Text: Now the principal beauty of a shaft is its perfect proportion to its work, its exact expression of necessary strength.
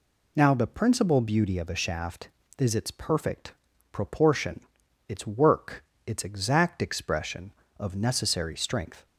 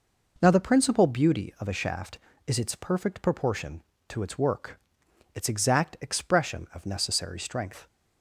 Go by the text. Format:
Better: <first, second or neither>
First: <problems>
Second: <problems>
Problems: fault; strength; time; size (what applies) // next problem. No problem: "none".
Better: second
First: pauses between "perfect" and "proportion"; at 3.5 s; 0.38 s long // skips "to"; at 4.8 s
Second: none